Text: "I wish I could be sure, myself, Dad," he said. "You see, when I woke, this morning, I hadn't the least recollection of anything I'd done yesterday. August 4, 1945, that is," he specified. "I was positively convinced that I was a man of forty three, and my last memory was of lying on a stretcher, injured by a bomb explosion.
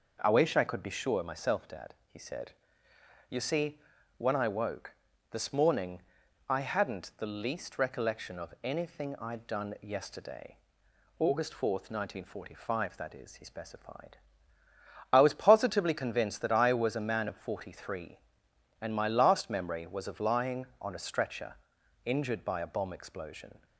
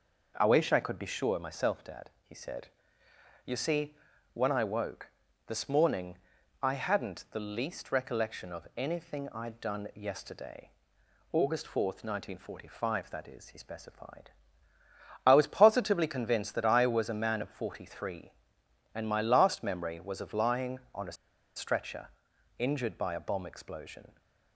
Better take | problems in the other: first | pauses between "a" and "stretcher"; at 21.1 s; 0.42 s long

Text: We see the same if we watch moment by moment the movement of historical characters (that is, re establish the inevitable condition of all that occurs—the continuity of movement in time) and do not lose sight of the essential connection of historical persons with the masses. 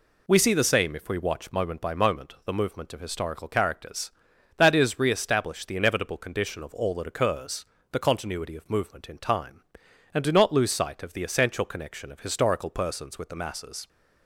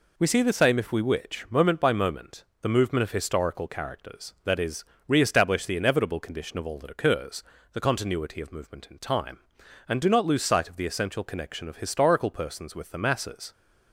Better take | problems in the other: first | says "witch" for "watch"; at 1.0 s // pauses between "moment" and "the"; slight; at 2.4 s; 0.16 s long

